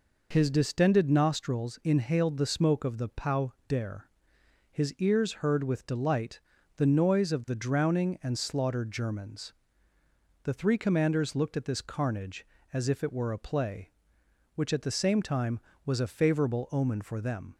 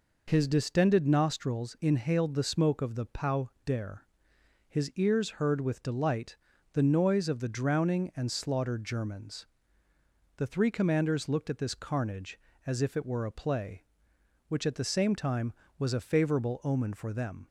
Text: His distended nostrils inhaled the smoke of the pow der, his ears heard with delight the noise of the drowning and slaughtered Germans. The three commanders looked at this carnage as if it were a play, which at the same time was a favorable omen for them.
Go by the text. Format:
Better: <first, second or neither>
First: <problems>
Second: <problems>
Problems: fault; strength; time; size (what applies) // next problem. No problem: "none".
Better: neither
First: pauses between "pow" and "der"; slight; at 3.5 s; 0.16 s long // pauses between "delight" and "the"; at 6.3 s; 0.38 s long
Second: pauses between "pow" and "der"; slight; at 3.4 s; 0.16 s long // pauses between "delight" and "the"; at 6.3 s; 0.38 s long